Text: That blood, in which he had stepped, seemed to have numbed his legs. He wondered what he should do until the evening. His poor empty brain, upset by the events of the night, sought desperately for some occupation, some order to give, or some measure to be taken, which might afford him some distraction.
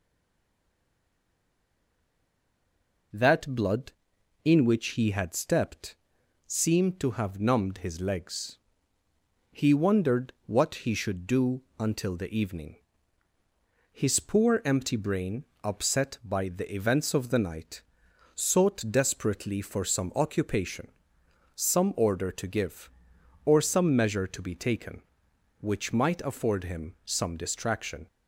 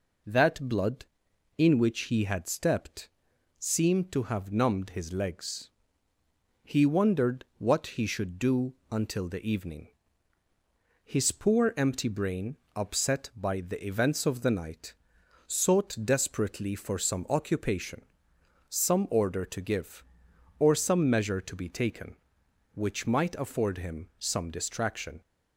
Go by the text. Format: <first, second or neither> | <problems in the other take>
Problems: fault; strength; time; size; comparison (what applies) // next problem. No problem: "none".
second | stays silent before the first word; strong; until 3.1 s; 3.1 s long // pauses between "do" and "until"; slight; at 11.6 s; 0.16 s long; slight in the second